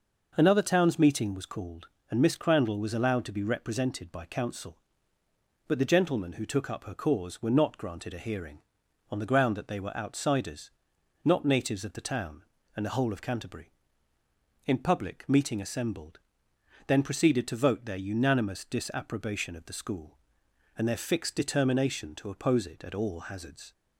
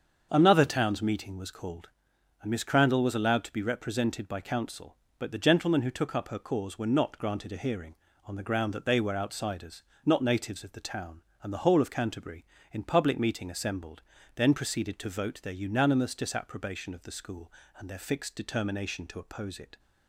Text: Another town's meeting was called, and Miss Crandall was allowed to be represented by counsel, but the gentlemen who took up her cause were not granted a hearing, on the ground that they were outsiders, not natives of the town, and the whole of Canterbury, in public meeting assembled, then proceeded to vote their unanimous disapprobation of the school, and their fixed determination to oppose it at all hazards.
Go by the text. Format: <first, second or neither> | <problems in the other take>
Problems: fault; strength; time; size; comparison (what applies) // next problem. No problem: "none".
first | starts louder than the rest; until 1.3 s; 7 dB // stops before "at all hazards"; at 19.7 s